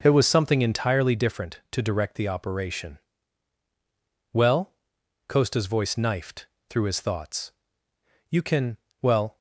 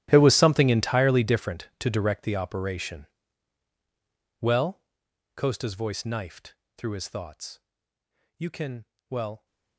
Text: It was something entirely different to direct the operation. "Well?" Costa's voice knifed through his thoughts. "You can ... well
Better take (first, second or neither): first